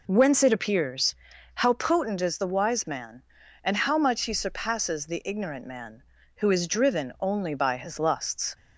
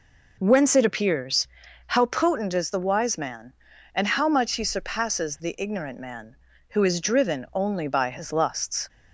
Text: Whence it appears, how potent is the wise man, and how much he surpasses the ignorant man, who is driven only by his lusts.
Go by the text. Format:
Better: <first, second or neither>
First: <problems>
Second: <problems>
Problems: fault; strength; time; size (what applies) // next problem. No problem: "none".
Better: neither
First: none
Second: none